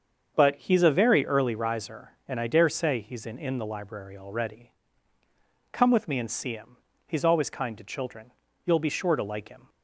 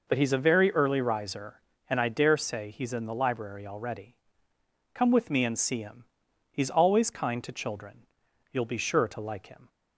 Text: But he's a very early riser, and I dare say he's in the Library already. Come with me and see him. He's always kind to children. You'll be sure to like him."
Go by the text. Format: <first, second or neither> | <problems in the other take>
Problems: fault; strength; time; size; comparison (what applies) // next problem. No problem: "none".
second | starts louder than the rest; until 1.3 s; 7 dB // says "in" twice; at 3.3 s